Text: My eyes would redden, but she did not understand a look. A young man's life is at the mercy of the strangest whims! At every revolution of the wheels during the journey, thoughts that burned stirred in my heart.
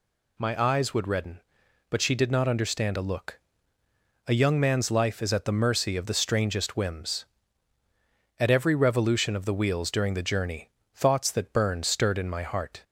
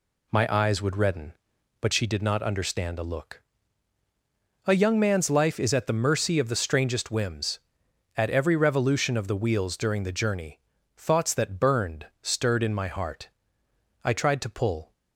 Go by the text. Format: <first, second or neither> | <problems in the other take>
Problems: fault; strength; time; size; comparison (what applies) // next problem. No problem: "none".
first | goes on to say "I tried to pull"; noticeable; from 14.0 s on; 0.90 s long